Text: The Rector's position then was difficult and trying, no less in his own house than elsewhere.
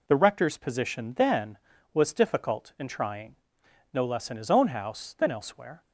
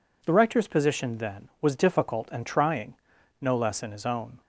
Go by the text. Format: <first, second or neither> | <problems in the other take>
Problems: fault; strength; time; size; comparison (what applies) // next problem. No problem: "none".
first | stops before "house than elsewhere"; at 4.4 s